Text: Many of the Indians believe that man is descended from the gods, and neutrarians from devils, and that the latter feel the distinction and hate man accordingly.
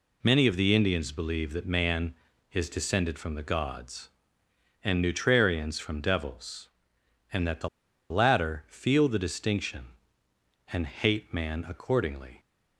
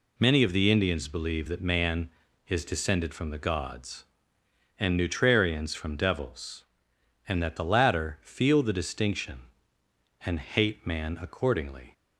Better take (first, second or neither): second